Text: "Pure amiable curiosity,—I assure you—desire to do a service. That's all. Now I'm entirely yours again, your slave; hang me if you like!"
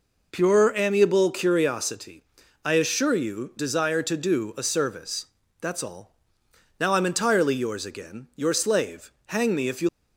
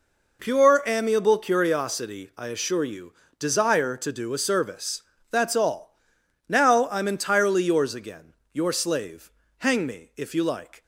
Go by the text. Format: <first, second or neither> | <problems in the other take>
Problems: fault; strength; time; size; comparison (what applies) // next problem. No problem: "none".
second | stops before "like"; at 9.8 s